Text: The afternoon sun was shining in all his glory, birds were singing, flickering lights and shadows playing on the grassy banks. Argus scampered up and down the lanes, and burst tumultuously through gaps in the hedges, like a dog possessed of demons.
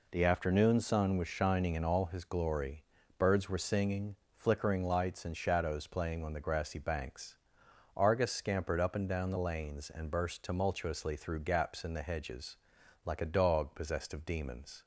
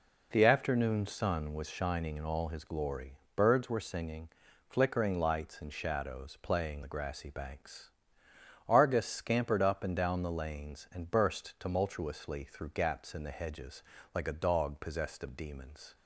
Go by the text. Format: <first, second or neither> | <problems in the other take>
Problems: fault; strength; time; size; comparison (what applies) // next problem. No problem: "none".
first | skips "on"; at 6.8 s